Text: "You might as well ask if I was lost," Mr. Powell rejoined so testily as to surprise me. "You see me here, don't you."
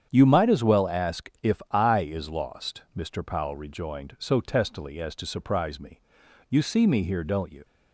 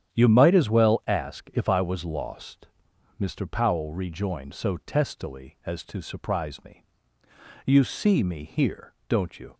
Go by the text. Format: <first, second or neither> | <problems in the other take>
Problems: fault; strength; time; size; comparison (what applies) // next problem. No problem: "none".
second | starts louder than the rest; strong; until 1.1 s; 8.5 dB; strong in the second // says "is" for "was"; at 1.9 s